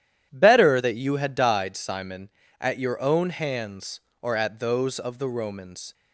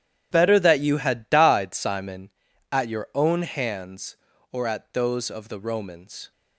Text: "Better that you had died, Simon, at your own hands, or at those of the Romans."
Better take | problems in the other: neither | starts louder than the rest; strong; the same in both

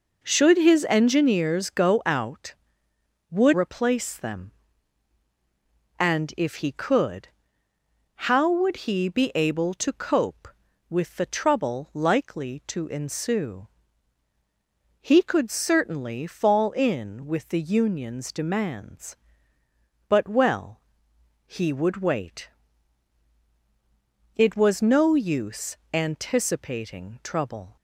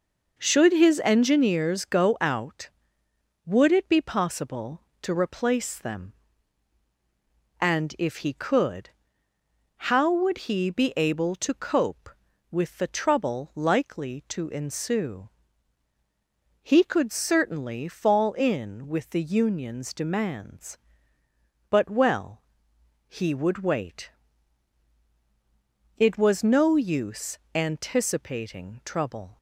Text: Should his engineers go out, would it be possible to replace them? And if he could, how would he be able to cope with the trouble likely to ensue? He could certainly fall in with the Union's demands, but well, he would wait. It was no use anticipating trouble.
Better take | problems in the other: second | skips "it be possible to"; at 3.5 s // pauses between "use" and "anticipating"; slight; at 25.7 s; 0.16 s long; slight in the second

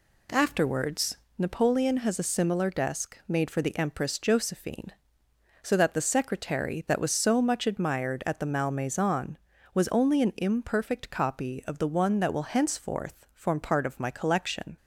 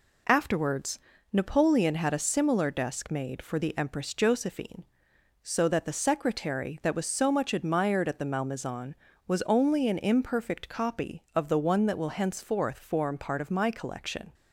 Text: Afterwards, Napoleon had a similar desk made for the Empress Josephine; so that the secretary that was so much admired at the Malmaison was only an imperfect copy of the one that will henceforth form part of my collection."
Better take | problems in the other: second | says "has" for "had"; at 1.9 s

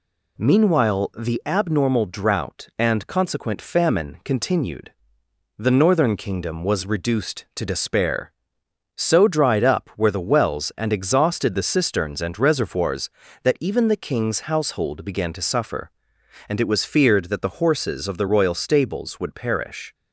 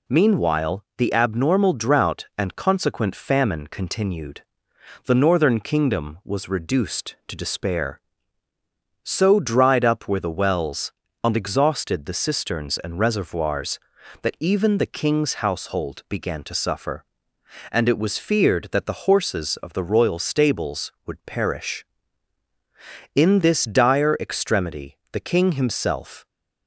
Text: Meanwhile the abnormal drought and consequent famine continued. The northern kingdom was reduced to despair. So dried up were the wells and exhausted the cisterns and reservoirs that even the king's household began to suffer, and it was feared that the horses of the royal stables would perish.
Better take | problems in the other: first | goes on to say "In this dire extremity the king himself"; strong; from 23.1 s on; 3.1 s long

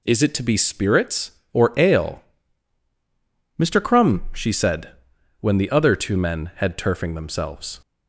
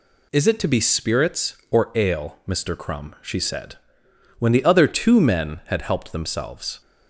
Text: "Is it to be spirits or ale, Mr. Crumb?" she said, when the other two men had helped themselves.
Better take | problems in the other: second | says "turfing" for "helped"; at 6.7 s

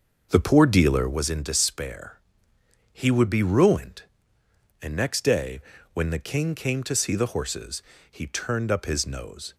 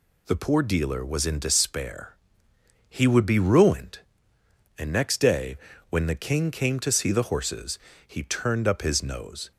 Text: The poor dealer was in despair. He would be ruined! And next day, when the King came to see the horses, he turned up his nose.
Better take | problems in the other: second | starts louder than the rest; noticeable; until 1.3 s; 6 dB

